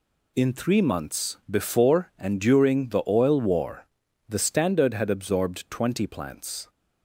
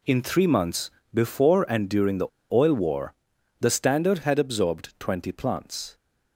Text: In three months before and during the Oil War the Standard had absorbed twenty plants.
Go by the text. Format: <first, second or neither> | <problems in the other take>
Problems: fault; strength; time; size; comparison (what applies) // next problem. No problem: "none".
first | pauses between "months" and "before"; slight; at 0.8 s; 0.24 s long // pauses between "the" and "Oil"; slight; at 2.2 s; 0.26 s long // pauses between "War" and "the"; noticeable; at 3.1 s; 0.48 s long; also in the first